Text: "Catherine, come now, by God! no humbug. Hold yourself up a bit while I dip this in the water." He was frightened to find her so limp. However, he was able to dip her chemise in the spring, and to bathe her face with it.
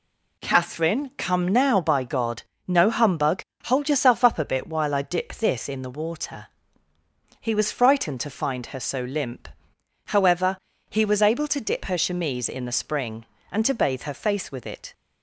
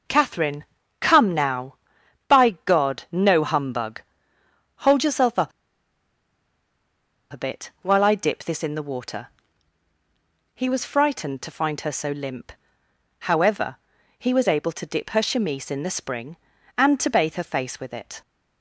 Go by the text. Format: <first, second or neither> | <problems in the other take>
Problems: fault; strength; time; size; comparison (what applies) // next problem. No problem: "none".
first | pauses between "up" and "a"; strong; at 5.5 s; 1.8 s long